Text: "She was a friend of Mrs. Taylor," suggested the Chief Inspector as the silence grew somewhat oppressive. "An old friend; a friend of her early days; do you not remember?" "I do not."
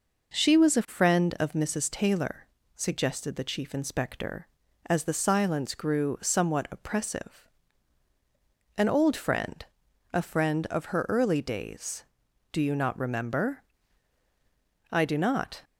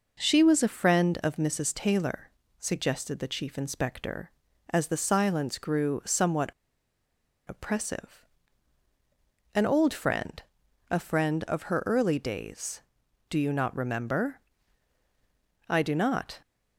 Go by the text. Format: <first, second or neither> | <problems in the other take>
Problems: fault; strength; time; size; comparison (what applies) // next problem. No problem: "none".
first | pauses between "somewhat" and "oppressive"; at 6.5 s; 0.99 s long